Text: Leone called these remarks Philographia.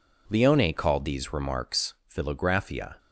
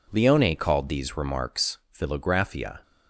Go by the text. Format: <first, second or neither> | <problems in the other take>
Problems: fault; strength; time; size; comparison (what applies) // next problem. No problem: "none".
neither | pauses between "remarks" and "Philographia"; slight; the same in both